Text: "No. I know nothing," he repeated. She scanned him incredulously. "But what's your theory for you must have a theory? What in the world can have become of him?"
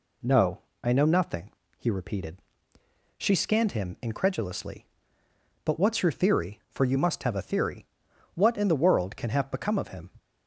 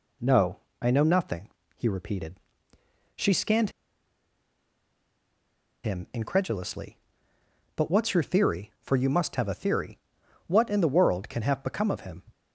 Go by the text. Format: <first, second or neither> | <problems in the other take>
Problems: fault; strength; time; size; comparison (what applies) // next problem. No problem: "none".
first | pauses between "scanned" and "him"; strong; at 3.7 s; 2.1 s long